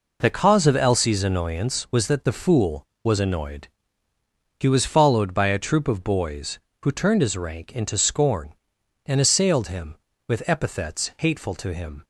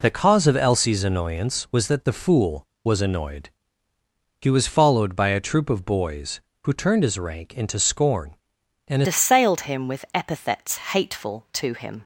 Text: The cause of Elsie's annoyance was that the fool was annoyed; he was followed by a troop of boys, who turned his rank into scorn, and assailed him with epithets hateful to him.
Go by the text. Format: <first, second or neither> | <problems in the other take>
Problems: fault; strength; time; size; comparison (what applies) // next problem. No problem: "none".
first | changes voice at "assailed"; from 9.0 s on; 3.0 s long